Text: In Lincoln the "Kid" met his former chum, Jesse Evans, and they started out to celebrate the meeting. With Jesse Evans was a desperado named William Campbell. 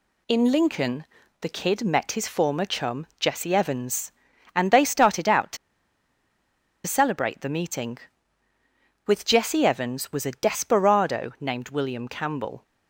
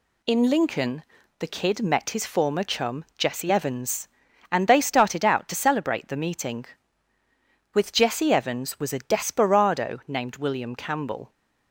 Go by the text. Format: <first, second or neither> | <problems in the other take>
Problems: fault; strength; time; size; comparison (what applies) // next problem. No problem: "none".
second | pauses between "Lincoln" and "the"; at 1.0 s; 0.38 s long; also in the second // pauses between "to" and "celebrate"; strong; at 5.5 s; 1.2 s long